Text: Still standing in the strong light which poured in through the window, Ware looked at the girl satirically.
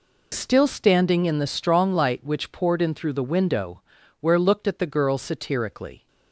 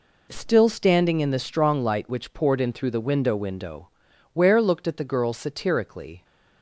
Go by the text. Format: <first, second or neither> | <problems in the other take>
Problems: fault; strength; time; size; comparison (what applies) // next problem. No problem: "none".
first | says "window" twice; at 3.3 s